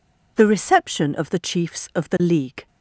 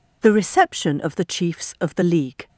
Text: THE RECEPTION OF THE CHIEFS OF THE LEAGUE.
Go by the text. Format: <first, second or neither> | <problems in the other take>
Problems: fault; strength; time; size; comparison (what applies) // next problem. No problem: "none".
neither | none